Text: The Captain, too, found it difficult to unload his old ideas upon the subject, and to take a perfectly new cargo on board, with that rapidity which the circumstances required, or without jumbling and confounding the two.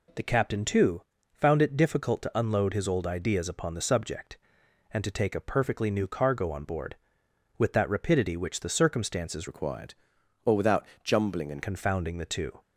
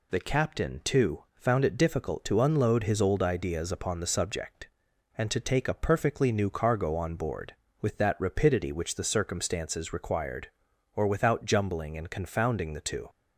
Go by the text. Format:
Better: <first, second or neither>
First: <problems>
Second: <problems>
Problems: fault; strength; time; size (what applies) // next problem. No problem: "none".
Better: second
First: changes voice from "required" to "and"; from 9.4 to 11.6 s; 2.2 s long // pauses between "without" and "jumbling"; slight; at 10.8 s; 0.20 s long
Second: none